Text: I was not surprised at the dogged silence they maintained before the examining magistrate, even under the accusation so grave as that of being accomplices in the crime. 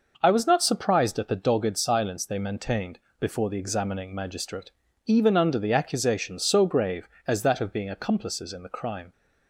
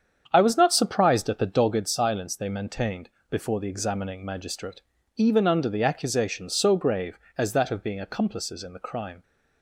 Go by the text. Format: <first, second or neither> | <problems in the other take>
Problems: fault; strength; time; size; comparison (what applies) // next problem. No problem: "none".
first | starts louder than the rest; strong; until 1.9 s; 8 dB // pauses between "maintained" and "before"; slight; at 3.1 s; 0.20 s long; slight in the first